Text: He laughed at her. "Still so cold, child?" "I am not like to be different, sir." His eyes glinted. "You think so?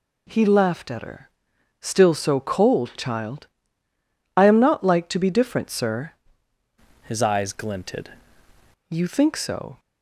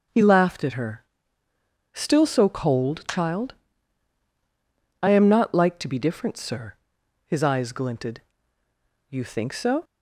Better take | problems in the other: second | changes voice from "His" to "glinted"; from 7.0 to 8.1 s; 1.1 s long

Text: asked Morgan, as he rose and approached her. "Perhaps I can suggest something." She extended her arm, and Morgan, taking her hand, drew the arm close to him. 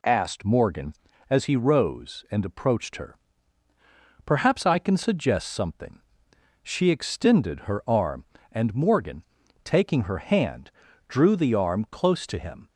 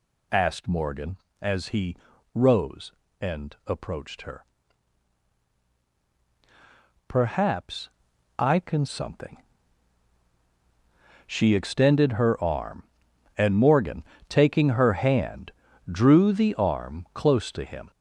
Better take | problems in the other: first | pauses between "he" and "rose"; at 1.9 s; 0.40 s long // pauses between "Perhaps" and "I"; noticeable; at 7.8 s; 0.48 s long // skips "suggest"; at 8.8 s

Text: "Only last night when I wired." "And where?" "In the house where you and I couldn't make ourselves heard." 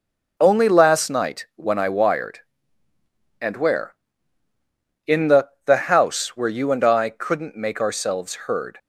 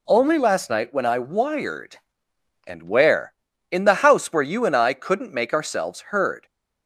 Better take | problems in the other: second | says "the" twice; at 5.6 s

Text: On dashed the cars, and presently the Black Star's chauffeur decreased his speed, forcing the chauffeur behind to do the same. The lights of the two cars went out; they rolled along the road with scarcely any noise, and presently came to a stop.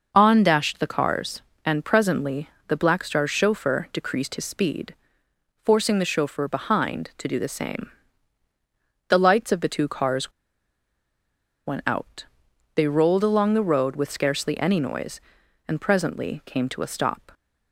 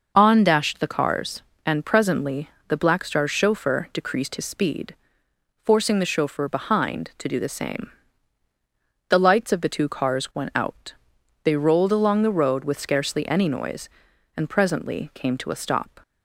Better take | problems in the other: second | pauses between "presently" and "the"; slight; at 2.4 s; 0.20 s long; slight in the second // pauses between "cars" and "went"; strong; at 10.3 s; 1.3 s long

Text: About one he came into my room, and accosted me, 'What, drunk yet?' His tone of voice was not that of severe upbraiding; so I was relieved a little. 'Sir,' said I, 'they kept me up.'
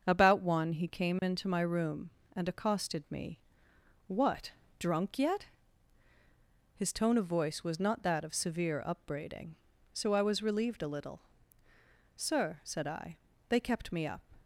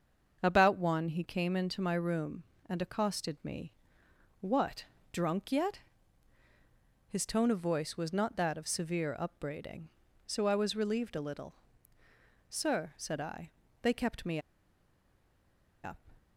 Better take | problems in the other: first | starts louder than the rest; until 1.4 s; 6.5 dB; also in the first // pauses between "me" and "up"; strong; at 14.3 s; 1.4 s long

